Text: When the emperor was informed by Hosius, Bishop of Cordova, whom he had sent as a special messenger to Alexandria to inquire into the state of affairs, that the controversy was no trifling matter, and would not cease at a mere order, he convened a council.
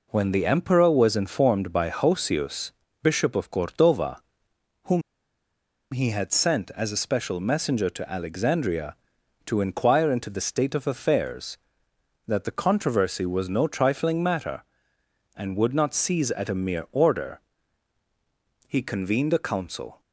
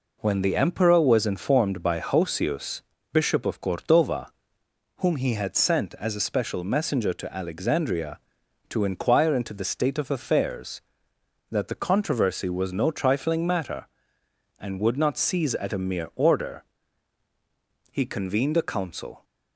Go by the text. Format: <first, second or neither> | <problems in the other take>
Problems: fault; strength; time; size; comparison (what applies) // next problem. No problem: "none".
second | pauses between "whom" and "he"; noticeable; at 5.0 s; 0.90 s long